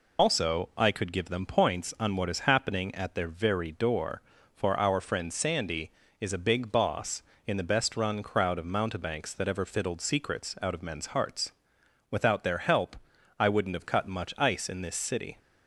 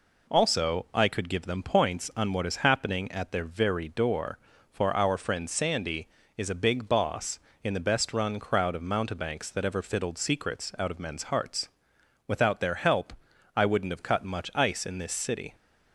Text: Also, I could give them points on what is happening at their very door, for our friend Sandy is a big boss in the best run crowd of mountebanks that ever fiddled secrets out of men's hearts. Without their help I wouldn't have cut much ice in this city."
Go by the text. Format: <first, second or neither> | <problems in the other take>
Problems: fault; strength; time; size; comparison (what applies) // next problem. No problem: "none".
second | loses the start of "Also"; at 0.1 s; 70 ms // pauses between "help" and "I"; at 12.9 s; 0.42 s long; also in the second